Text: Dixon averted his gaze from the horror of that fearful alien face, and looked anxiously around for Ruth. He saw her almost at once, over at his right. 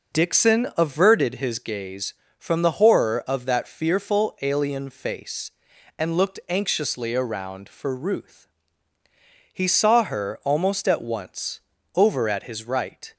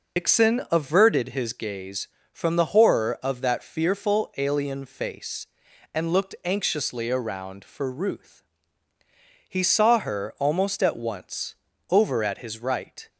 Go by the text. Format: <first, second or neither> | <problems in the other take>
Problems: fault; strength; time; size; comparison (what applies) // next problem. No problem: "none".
first | loses the start of "Dixon"; at 0.1 s; 95 ms